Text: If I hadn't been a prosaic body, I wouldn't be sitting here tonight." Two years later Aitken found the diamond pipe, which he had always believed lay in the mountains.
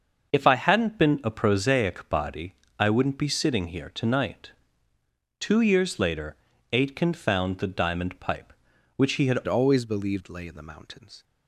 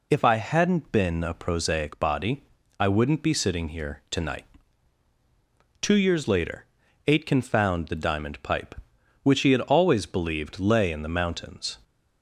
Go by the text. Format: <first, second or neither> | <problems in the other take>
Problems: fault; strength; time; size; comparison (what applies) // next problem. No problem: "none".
second | starts louder than the rest; until 1.3 s; 6.5 dB // pauses between "later" and "Aitken"; at 6.3 s; 0.38 s long; also in the second // changes voice at "always"; from 9.4 s on; 1.8 s long